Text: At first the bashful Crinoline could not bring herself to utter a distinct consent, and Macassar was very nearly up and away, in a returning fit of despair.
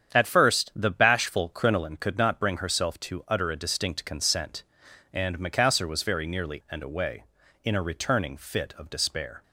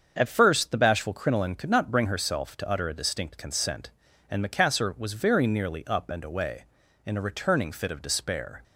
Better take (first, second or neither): second